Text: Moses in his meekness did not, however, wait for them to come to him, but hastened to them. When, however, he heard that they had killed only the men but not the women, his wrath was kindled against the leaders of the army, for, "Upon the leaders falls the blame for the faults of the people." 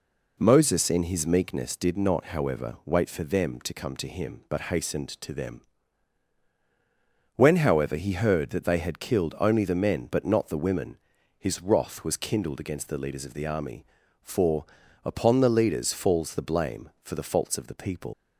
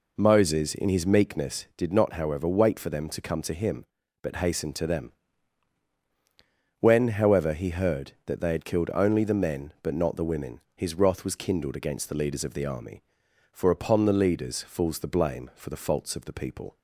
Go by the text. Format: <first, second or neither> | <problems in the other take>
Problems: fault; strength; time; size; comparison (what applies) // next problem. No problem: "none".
second | leaves "people" unfinished; at 18.1 s; 110 ms